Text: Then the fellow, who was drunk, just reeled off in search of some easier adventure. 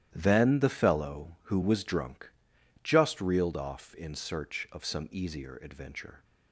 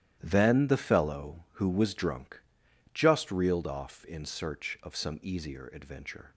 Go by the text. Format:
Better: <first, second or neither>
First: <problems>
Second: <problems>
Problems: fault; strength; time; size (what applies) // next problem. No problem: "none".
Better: neither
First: starts louder than the rest; strong; until 1.1 s; 12 dB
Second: starts louder than the rest; strong; until 1.2 s; 12 dB